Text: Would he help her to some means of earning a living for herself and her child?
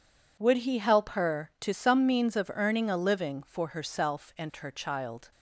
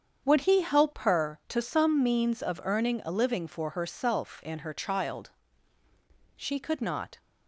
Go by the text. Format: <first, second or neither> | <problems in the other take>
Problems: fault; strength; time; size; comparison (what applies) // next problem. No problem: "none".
first | starts louder than the rest; strong; until 1.3 s; 7.5 dB // goes on to say "She could not"; noticeable; from 6.3 s on; 0.84 s long